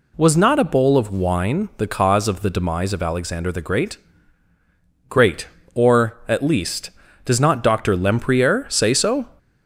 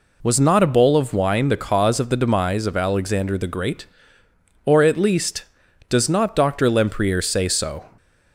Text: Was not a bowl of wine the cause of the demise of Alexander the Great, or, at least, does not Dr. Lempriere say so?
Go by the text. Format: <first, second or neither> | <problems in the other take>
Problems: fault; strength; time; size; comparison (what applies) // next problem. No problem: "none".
second | says "Great" twice; at 5.0 s